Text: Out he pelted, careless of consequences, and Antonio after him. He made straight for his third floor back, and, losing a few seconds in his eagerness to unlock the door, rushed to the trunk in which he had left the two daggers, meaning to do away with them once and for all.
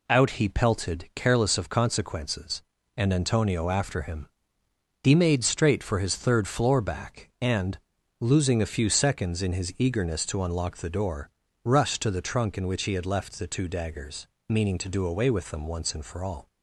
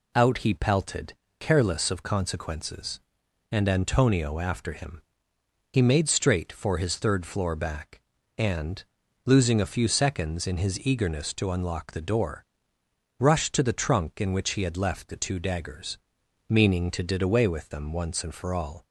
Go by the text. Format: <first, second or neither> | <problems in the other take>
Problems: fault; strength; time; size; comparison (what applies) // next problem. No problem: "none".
first | says "did" for "do"; at 17.0 s